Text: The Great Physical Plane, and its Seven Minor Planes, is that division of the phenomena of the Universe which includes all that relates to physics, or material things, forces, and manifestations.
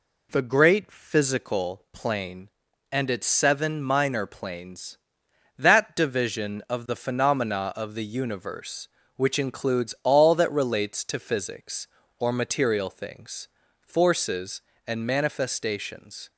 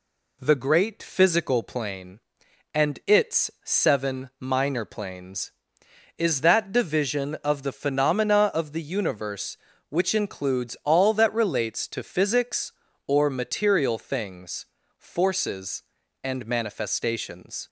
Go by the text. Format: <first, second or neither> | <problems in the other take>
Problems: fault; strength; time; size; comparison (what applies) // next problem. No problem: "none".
second | skips "is"; at 5.2 s